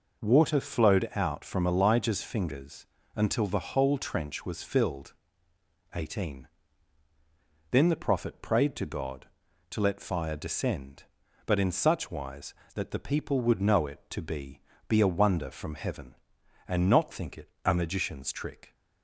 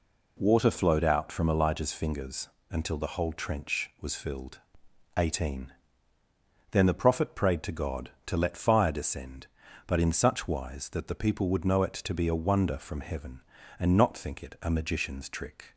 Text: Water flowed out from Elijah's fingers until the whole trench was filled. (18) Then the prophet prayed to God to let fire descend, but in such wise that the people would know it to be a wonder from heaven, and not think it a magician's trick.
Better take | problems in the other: second | pauses between "fingers" and "until"; slight; at 2.8 s; 0.28 s long; slight in the second // says "be" twice; at 14.8 s

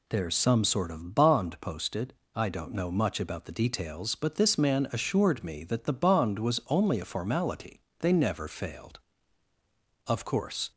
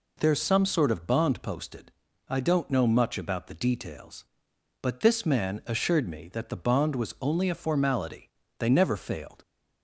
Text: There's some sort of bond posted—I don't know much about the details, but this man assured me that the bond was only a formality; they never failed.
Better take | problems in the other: second | goes on to say "Of course"; noticeable; from 10.0 s on; 0.64 s long

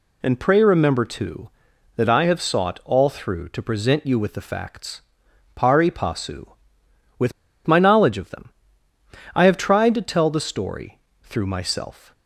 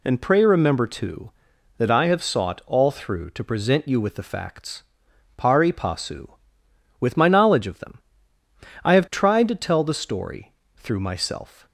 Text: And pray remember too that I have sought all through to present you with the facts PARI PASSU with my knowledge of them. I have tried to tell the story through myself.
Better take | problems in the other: second | pauses between "facts" and "PARI"; noticeable; at 5.0 s; 0.54 s long; noticeable in the second // pauses between "with" and "my"; slight; at 7.3 s; 0.34 s long // pauses between "story" and "through"; slight; at 10.9 s; 0.24 s long; slight in the second

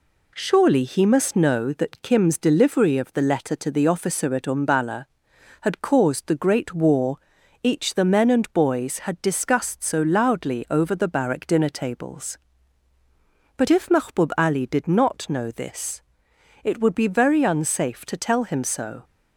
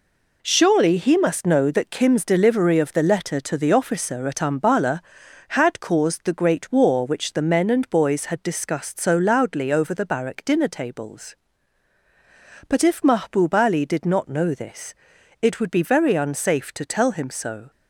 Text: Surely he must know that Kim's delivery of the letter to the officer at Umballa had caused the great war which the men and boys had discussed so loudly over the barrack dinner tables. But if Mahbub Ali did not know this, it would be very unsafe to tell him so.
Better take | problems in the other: second | says "each" for "which"; at 7.6 s

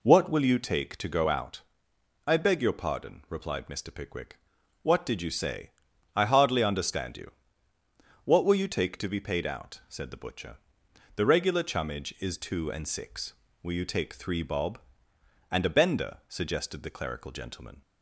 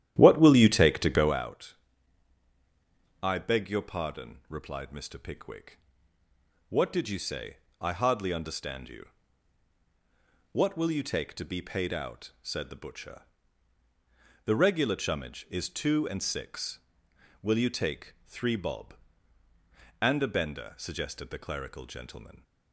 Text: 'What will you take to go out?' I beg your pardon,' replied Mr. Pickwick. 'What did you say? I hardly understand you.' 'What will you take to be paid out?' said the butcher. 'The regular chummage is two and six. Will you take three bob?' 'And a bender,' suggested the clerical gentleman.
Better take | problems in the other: first | starts louder than the rest; strong; until 1.4 s; 11.5 dB

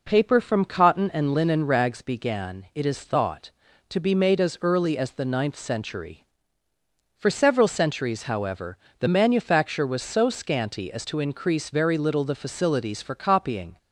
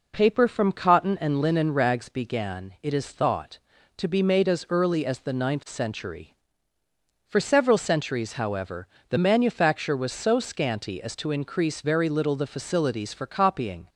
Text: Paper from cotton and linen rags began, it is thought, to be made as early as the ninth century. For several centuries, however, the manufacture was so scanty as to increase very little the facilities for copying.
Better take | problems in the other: neither | none

